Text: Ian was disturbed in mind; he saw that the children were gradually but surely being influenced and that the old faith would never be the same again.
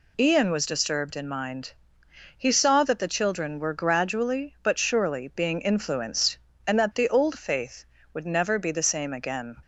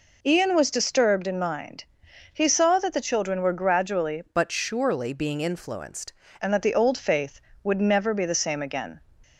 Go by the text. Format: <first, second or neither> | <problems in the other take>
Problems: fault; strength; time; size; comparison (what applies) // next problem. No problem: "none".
first | changes voice from "but" to "influenced"; from 4.2 to 6.1 s; 1.9 s long